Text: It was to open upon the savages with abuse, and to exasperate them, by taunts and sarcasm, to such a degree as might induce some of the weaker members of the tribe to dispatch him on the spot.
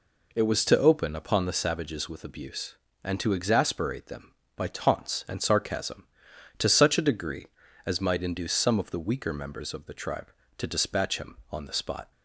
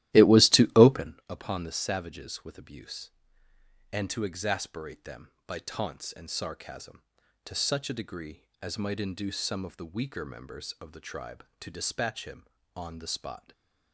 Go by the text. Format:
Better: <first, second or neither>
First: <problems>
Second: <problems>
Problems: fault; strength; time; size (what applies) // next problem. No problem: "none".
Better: first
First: none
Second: starts louder than the rest; strong; until 1.1 s; 15 dB